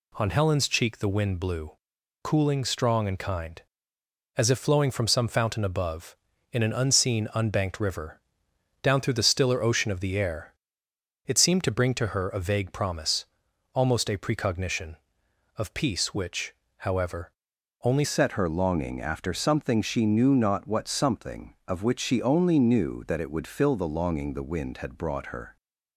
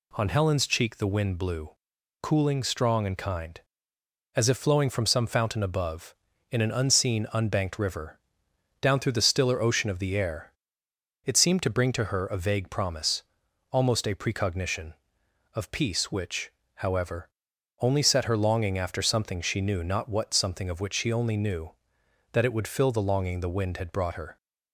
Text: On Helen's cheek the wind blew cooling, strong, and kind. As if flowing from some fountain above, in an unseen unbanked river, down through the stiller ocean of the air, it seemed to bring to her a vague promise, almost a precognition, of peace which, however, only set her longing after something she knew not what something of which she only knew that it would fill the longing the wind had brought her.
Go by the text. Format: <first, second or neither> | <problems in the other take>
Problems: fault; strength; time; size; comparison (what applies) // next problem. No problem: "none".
second | pauses between "blew" and "cooling"; noticeable; at 1.7 s; 0.52 s long; noticeable in the second // changes voice at "set"; from 18.0 s on; 7.5 s long